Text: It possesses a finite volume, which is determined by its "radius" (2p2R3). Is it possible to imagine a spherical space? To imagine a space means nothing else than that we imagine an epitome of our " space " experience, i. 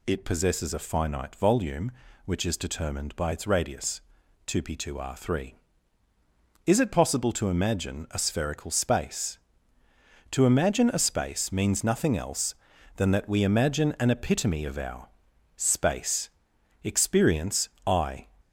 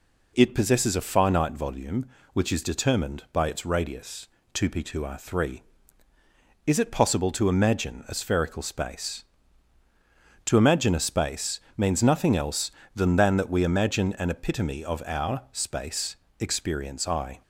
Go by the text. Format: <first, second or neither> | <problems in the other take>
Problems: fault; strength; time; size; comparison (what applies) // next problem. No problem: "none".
first | pauses between "space" and "means"; slight; at 11.5 s; 0.18 s long // says "than" twice; at 13.1 s